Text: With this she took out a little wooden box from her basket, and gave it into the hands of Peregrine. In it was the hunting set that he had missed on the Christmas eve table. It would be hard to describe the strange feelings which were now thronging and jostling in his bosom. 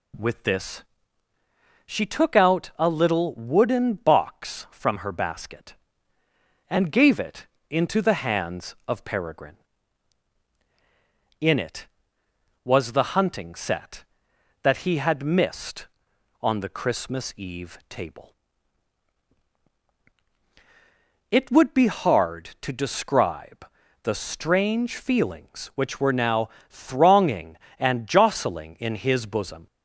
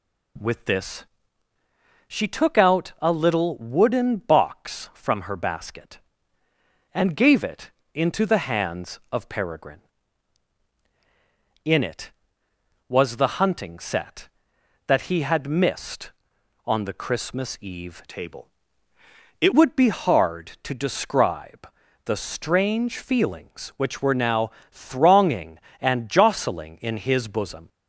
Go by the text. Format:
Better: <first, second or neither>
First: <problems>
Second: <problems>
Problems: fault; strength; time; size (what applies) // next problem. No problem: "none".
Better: first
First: pauses between "this" and "she"; at 0.8 s; 1.0 s long // pauses between "it" and "into"; slight; at 7.4 s; 0.24 s long // pauses between "describe" and "the"; at 23.6 s; 0.38 s long // pauses between "now" and "thronging"; slight; at 26.4 s; 0.20 s long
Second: pauses between "this" and "she"; at 1.0 s; 1.0 s long // pauses between "it" and "into"; slight; at 7.7 s; 0.24 s long // changes voice from "table" to "It"; from 18.0 to 19.5 s; 1.5 s long // pauses between "describe" and "the"; at 21.6 s; 0.38 s long // pauses between "now" and "thronging"; slight; at 24.5 s; 0.20 s long